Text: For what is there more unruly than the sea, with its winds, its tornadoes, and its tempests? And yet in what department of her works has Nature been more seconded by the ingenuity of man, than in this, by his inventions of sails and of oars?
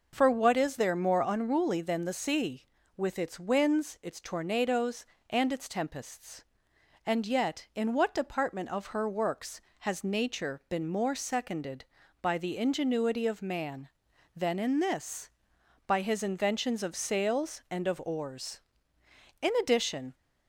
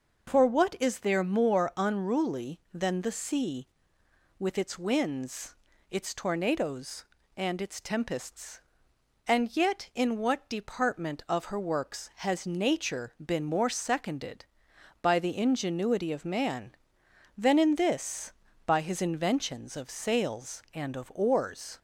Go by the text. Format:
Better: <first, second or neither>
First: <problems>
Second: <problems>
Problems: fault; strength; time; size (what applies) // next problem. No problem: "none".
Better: second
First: goes on to say "In addition"; noticeable; from 19.4 s on; 0.72 s long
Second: none